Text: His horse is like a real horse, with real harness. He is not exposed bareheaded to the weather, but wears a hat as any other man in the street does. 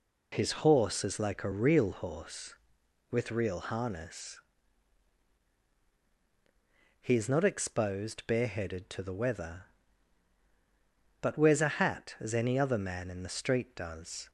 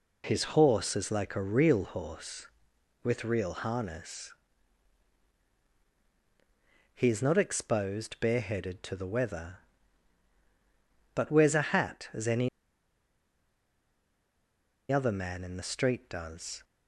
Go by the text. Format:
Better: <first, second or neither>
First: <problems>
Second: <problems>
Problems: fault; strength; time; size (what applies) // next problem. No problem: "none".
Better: first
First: none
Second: pauses between "any" and "other"; strong; at 12.4 s; 2.4 s long